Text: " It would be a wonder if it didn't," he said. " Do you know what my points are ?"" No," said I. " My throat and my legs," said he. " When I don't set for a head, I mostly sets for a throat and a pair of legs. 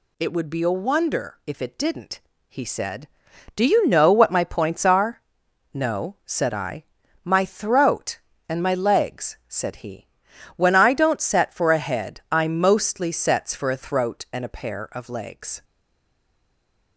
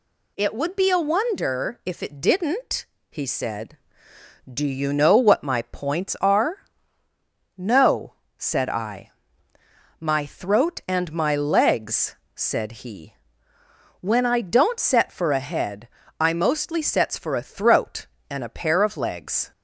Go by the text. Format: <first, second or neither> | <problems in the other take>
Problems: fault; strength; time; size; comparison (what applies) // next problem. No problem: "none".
second | stays silent after the last word; noticeable; from 15.6 s on; 1.3 s long